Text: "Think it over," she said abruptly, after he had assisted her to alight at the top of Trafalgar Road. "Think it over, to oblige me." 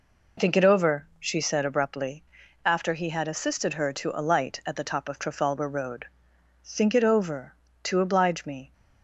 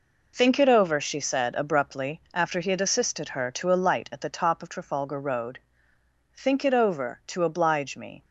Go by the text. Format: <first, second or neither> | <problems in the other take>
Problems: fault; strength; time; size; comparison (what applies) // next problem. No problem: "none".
neither | none